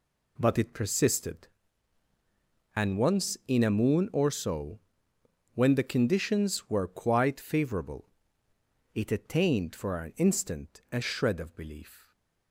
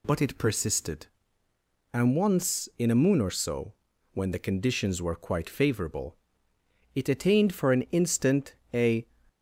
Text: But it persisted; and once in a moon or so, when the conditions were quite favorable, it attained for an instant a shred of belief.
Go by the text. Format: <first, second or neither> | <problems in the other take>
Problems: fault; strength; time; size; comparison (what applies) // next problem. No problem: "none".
first | pauses between "instant" and "a"; slight; at 8.5 s; 0.18 s long // stops before "shred of belief"; at 9.2 s